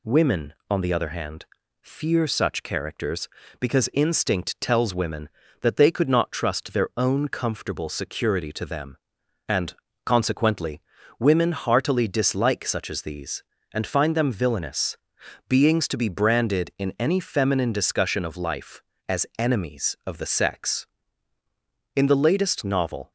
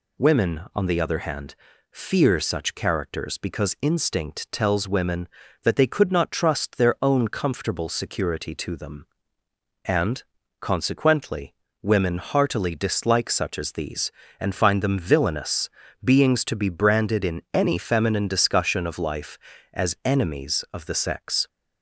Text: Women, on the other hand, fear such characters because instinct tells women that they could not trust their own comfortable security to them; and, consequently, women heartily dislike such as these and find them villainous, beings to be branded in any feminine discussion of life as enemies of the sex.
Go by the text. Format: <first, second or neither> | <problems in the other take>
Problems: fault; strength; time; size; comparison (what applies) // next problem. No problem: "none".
second | goes on to say "In the latest novel"; noticeable; from 21.9 s on; 1.1 s long